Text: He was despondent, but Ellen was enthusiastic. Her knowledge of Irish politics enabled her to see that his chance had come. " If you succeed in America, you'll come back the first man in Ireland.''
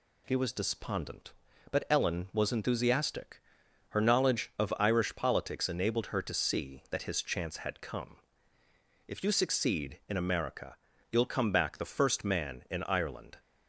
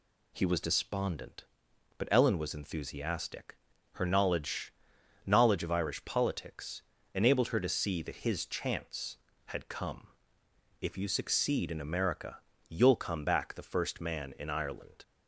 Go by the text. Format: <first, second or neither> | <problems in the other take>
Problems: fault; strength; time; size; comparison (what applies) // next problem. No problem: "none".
first | says "knowledge" twice; at 5.2 s // pauses between "politics" and "enabled"; slight; at 6.8 s; 0.32 s long